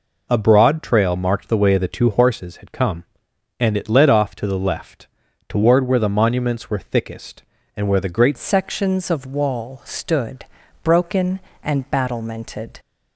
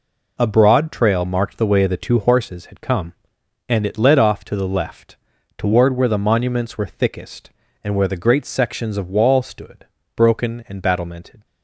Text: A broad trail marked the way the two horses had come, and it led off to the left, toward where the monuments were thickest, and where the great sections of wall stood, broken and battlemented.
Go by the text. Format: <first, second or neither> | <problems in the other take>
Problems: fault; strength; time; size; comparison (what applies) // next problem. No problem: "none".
second | changes voice at "sections"; from 8.3 s on; 4.4 s long